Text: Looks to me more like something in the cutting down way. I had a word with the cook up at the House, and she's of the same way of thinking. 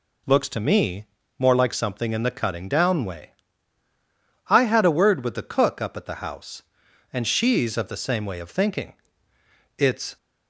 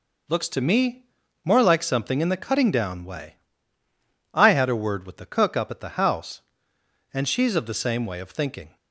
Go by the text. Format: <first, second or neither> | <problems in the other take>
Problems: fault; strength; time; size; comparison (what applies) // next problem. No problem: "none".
second | pauses between "me" and "more"; slight; at 1.0 s; 0.32 s long; also in the second // goes on to say "It's"; slight; from 9.7 s on; 0.40 s long